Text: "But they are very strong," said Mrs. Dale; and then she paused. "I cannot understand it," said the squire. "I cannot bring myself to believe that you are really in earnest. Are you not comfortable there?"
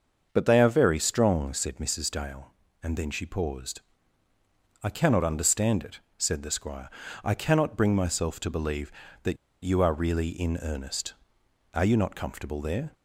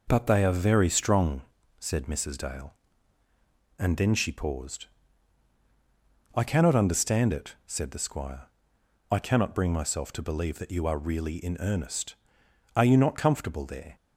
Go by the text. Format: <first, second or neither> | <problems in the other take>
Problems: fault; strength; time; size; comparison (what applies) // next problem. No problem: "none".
second | starts louder than the rest; until 1.3 s; 6.5 dB // pauses between "that" and "you"; slight; at 9.3 s; 0.28 s long